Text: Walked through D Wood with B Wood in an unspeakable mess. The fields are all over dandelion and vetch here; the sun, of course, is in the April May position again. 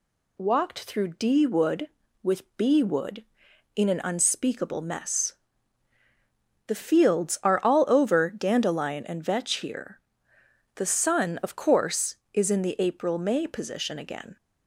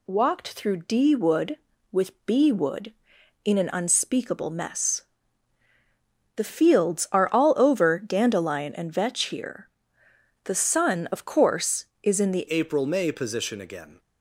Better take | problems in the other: first | changes voice at "April"; from 12.4 s on; 1.5 s long

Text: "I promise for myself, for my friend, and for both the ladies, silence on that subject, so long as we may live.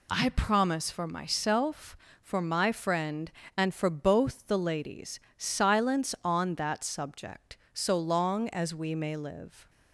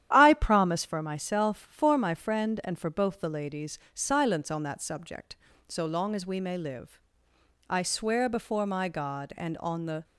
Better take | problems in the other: first | starts louder than the rest; strong; until 1.1 s; 10.5 dB // goes on to say "I swear before my God and on the"; strong; from 7.6 s on; 2.3 s long

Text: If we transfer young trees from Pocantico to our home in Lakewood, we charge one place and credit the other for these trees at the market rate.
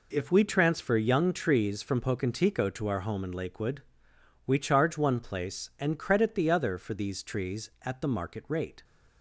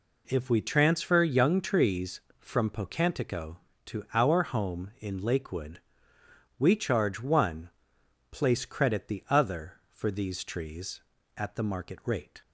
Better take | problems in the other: first | pauses between "one" and "place"; noticeable; at 7.6 s; 0.62 s long // skips "and"; at 8.6 s

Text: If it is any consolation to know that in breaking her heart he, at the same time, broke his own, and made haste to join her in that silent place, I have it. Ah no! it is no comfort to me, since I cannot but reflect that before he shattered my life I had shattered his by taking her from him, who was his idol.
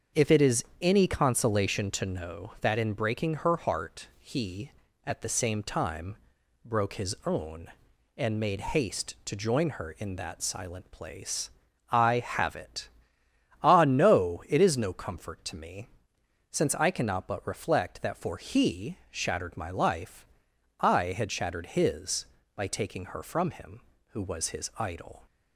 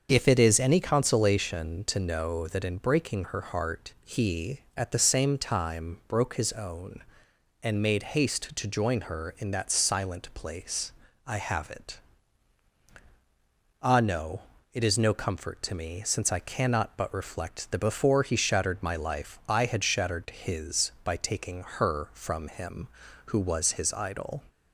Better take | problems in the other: second | starts louder than the rest; until 1.2 s; 7 dB; also in the second // pauses between "is" and "any"; slight; at 0.6 s; 0.16 s long // says "for" for "before"; at 18.1 s // pauses between "life" and "I"; noticeable; at 20.2 s; 0.52 s long

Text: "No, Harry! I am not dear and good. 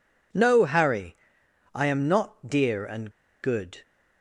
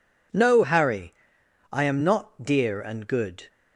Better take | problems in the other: second | pauses between "and" and "good"; slight; at 3.1 s; 0.31 s long

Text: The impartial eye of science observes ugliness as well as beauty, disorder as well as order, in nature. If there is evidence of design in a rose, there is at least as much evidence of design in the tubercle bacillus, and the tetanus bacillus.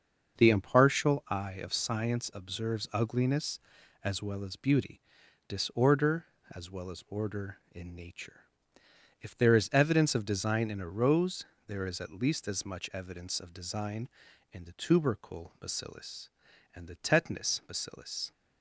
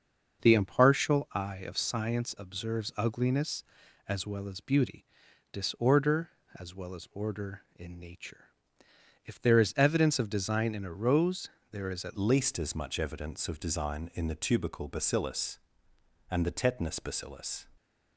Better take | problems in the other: first | starts louder than the rest; until 1.4 s; 6.5 dB; also in the first // changes voice at "least"; from 12.1 s on; 5.5 s long

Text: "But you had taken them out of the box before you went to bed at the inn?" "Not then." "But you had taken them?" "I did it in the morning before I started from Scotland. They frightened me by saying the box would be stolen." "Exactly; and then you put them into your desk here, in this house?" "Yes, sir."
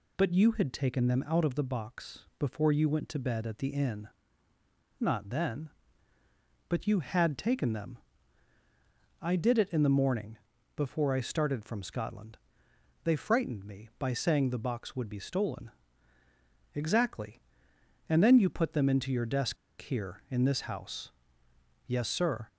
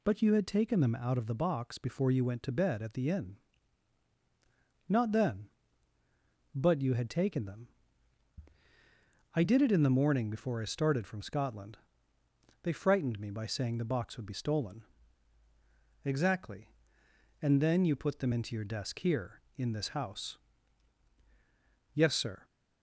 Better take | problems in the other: second | pauses between "box" and "before"; slight; at 2.1 s; 0.20 s long // pauses between "morning" and "before"; at 10.3 s; 0.40 s long // pauses between "desk" and "here"; slight; at 19.5 s; 0.25 s long

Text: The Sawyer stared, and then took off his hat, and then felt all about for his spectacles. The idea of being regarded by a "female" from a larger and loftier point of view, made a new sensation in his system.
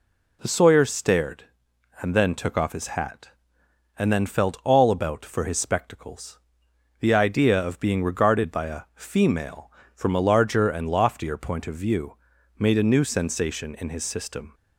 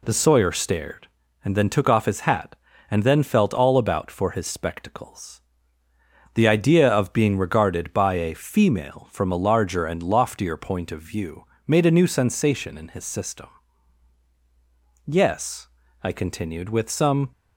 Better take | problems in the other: first | goes on to say "Yes I continued with some"; strong; from 15.0 s on; 2.2 s long

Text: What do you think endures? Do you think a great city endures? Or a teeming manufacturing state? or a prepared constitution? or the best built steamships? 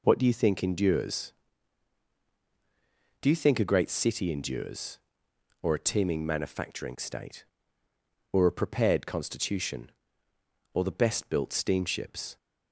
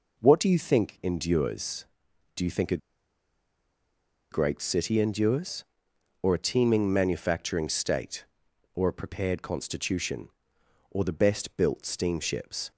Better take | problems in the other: first | pauses between "a" and "great"; strong; at 2.7 s; 1.5 s long

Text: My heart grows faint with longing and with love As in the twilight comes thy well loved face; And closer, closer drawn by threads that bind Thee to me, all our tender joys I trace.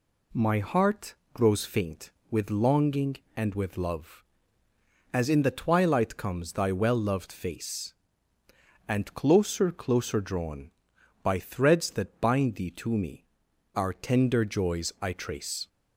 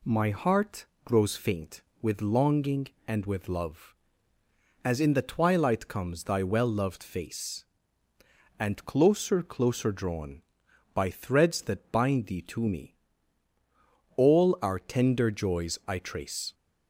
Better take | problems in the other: second | pauses between "heart" and "grows"; slight; at 1.1 s; 0.20 s long; slight in the second // skips "all"; at 13.4 s

